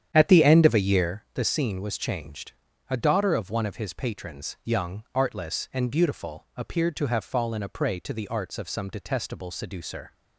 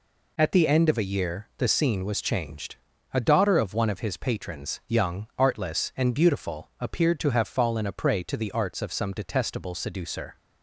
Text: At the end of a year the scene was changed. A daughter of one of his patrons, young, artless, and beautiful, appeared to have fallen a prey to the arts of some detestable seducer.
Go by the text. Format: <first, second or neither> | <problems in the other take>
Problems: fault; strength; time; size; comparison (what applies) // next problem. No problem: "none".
second | starts louder than the rest; strong; until 1.2 s; 9.5 dB